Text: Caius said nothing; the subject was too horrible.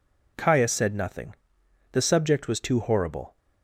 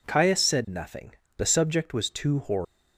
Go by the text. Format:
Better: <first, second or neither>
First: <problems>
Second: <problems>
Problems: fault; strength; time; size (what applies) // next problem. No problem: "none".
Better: neither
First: none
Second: none